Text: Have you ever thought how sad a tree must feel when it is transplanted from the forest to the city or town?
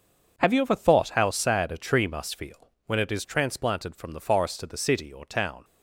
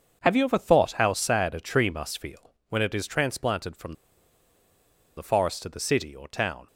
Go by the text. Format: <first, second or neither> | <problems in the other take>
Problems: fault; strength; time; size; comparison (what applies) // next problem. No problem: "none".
first | starts louder than the rest; until 1.2 s; 6.5 dB; also in the first // pauses between "feel" and "when"; slight; at 2.5 s; 0.16 s long; slight in the first // pauses between "from" and "the"; at 3.9 s; 1.2 s long